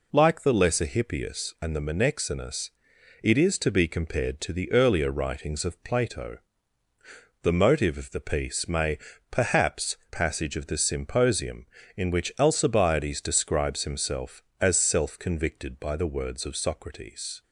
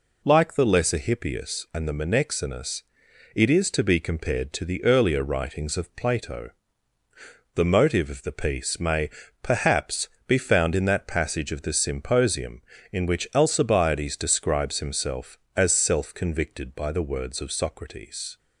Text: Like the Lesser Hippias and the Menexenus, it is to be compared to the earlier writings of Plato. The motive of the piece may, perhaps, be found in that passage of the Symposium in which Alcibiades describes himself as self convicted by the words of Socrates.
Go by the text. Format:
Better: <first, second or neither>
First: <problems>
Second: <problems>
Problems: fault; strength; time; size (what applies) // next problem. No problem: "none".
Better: second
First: skips "be found in that"; at 10.0 s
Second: none